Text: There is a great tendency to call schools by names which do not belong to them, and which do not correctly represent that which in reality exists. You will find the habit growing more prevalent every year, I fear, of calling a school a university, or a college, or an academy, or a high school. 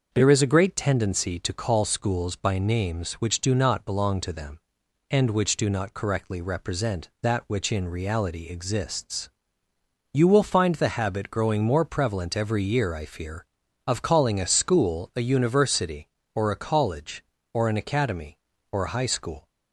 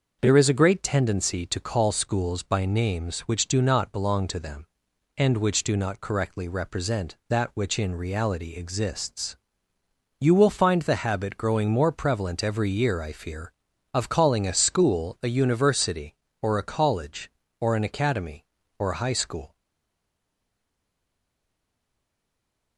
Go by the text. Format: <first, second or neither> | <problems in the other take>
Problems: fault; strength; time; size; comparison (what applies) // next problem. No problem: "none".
first | starts louder than the rest; noticeable; until 1.2 s; 6 dB; noticeable in the first // stays silent after the last word; strong; from 19.5 s on; 3.2 s long